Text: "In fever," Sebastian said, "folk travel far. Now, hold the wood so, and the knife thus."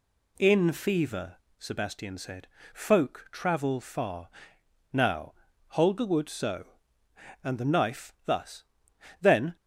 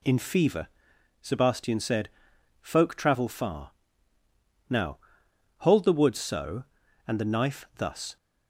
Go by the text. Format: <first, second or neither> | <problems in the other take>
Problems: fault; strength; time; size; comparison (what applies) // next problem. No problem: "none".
second | goes on to say "Then"; slight; from 9.2 s on; 0.34 s long